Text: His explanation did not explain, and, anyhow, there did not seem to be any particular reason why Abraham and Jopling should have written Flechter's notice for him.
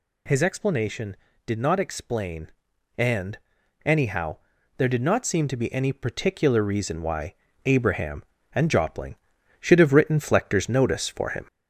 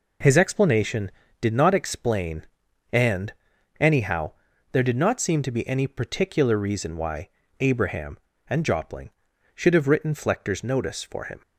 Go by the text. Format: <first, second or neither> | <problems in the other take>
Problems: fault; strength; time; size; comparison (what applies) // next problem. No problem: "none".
second | gets louder; slight; throughout; 2 dB // pauses between "why" and "Abraham"; slight; at 7.3 s; 0.30 s long; slight in the second